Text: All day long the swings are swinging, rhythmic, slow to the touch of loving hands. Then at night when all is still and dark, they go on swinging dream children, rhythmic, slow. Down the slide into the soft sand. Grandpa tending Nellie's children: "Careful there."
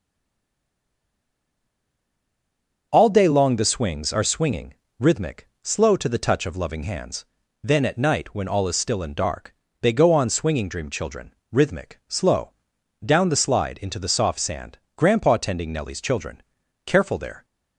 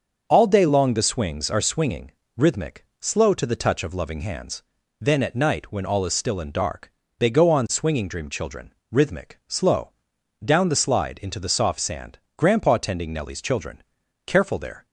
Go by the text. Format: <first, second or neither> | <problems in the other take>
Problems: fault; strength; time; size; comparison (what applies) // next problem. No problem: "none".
second | stays silent before the first word; strong; until 2.9 s; 2.9 s long // starts louder than the rest; until 3.9 s; 6.5 dB; also in the second